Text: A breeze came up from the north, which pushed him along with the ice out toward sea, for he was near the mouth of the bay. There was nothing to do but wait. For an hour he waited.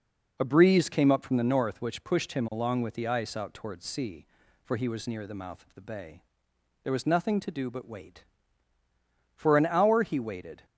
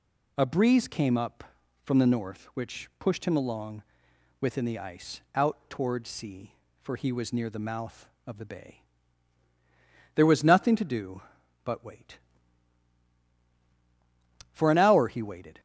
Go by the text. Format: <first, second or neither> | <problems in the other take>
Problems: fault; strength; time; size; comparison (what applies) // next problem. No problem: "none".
first | says "within" for "with"; at 4.3 s